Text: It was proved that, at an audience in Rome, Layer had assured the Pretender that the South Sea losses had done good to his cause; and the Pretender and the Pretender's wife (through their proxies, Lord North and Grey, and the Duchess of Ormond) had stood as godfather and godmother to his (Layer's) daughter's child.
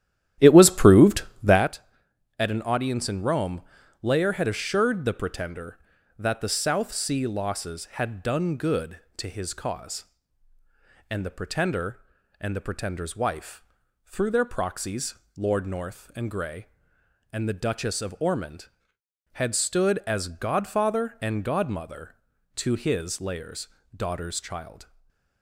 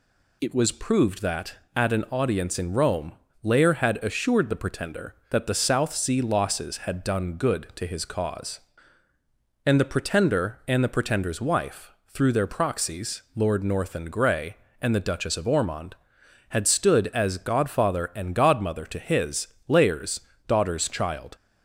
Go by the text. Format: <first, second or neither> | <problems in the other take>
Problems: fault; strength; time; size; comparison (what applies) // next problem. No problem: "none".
second | starts louder than the rest; strong; until 1.7 s; 12 dB // stays silent after the last word; slight; from 24.8 s on; 0.6 s long